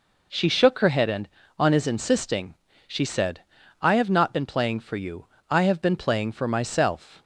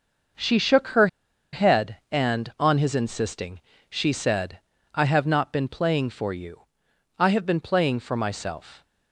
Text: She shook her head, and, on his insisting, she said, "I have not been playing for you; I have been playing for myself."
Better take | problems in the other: first | starts louder than the rest; until 1.8 s; 6 dB // pauses between "her" and "head"; noticeable; at 1.0 s; 0.46 s long

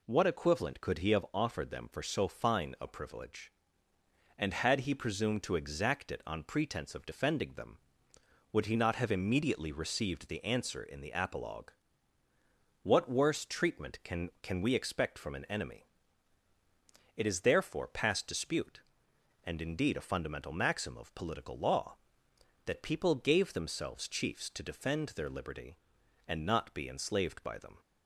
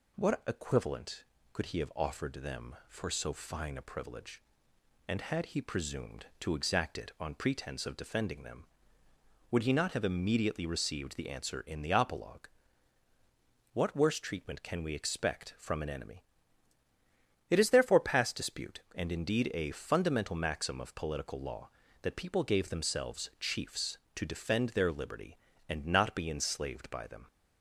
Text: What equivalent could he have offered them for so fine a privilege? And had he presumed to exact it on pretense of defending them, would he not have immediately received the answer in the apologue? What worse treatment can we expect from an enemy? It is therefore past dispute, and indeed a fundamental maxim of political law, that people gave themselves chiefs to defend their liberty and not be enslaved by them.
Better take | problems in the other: second | says "can" twice; at 14.4 s

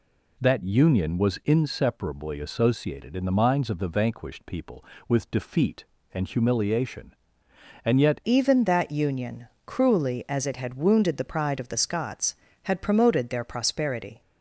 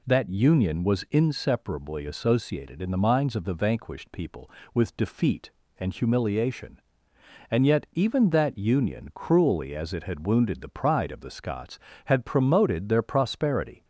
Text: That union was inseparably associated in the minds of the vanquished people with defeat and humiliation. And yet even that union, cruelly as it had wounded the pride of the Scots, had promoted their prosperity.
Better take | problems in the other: second | changes voice at "even"; from 8.2 s on; 6.0 s long

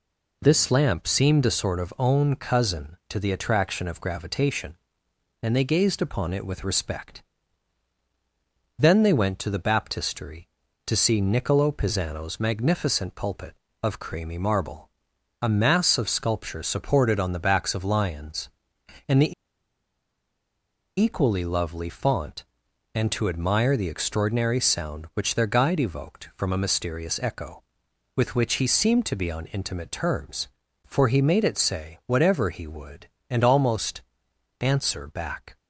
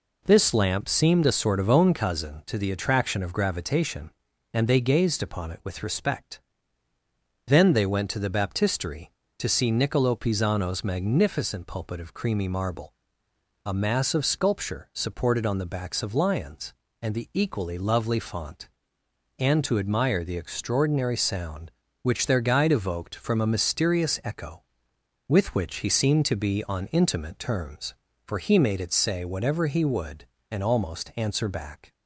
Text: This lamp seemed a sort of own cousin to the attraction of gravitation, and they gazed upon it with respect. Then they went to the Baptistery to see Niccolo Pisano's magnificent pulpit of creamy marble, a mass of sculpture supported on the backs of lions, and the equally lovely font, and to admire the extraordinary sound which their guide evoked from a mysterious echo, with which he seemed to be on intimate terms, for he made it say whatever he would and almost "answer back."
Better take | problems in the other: second | pauses between "the" and "equally"; strong; at 19.3 s; 1.6 s long // pauses between "almost" and "answer"; noticeable; at 34.0 s; 0.58 s long

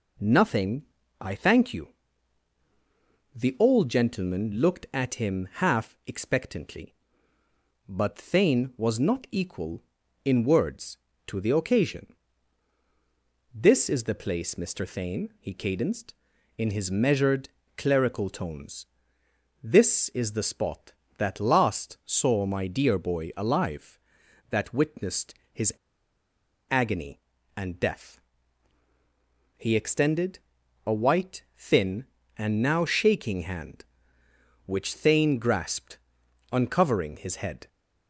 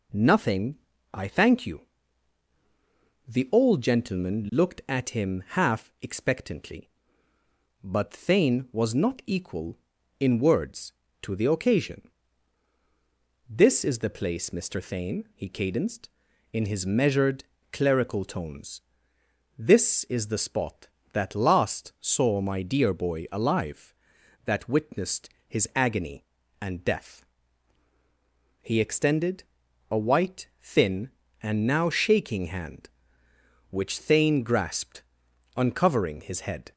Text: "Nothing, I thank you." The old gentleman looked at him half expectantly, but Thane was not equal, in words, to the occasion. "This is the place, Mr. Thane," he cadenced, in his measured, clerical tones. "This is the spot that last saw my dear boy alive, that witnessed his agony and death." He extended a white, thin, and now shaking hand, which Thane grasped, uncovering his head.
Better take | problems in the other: second | pauses between "witnessed" and "his"; slight; at 25.3 s; 0.18 s long; slight in the second // pauses between "his" and "agony"; at 25.7 s; 0.98 s long // pauses between "extended" and "a"; noticeable; at 30.3 s; 0.46 s long; noticeable in the second

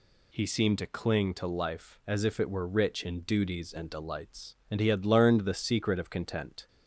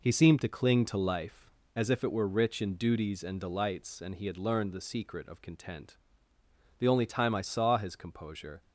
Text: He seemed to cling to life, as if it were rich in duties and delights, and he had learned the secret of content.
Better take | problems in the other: first | goes on to say "The only time I saw his composure"; strong; from 6.7 s on; 1.8 s long

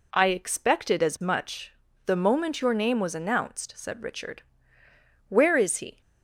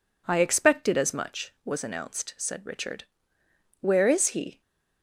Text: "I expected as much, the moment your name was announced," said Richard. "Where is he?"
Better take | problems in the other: first | skips "the moment your name"; at 1.5 s

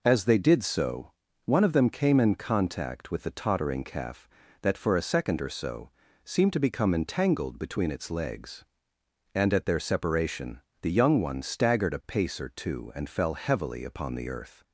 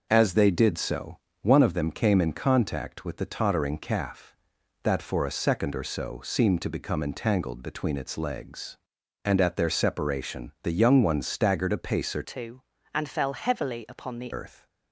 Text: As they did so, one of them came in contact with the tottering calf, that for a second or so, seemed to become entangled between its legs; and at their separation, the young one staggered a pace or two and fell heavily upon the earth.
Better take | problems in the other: first | changes voice from "two" to "the"; from 12.2 to 14.3 s; 2.1 s long

